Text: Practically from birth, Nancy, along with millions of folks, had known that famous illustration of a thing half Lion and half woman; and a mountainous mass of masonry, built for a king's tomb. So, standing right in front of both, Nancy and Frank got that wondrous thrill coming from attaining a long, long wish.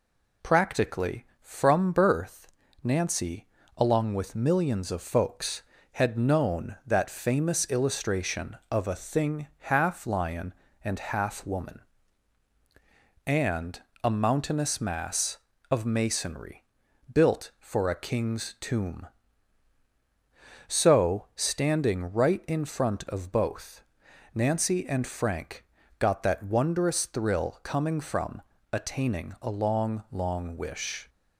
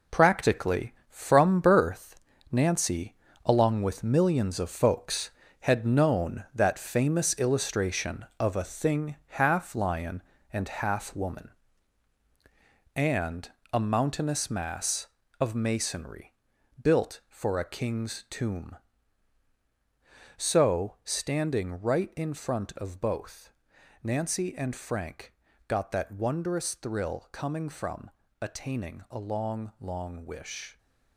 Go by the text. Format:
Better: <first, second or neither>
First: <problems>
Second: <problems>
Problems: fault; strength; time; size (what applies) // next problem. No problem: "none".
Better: first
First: pauses between "and" and "a"; slight; at 13.8 s; 0.20 s long // pauses between "Frank" and "got"; slight; at 25.6 s; 0.34 s long // pauses between "from" and "attaining"; slight; at 28.4 s; 0.30 s long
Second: gets quieter; strong; throughout; 8.5 dB // pauses between "and" and "a"; slight; at 13.5 s; 0.20 s long // pauses between "Frank" and "got"; slight; at 25.3 s; 0.34 s long // pauses between "from" and "attaining"; slight; at 28.0 s; 0.30 s long